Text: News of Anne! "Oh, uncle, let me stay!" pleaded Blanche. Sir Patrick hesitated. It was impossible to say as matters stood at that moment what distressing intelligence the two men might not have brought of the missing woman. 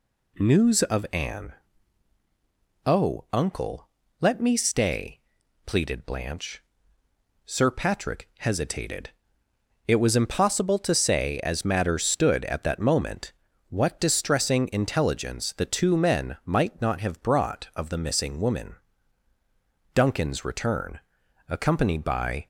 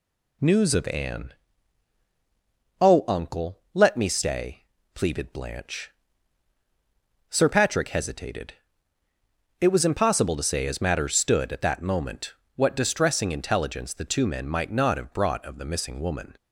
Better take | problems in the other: second | pauses between "moment" and "what"; slight; at 13.3 s; 0.36 s long; slight in the second // goes on to say "Duncan's return accompanied by"; strong; from 19.9 s on; 2.5 s long

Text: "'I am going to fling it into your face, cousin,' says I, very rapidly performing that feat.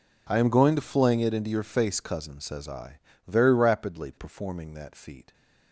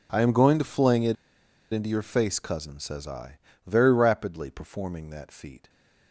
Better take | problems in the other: first | pauses between "it" and "into"; noticeable; at 1.1 s; 0.57 s long

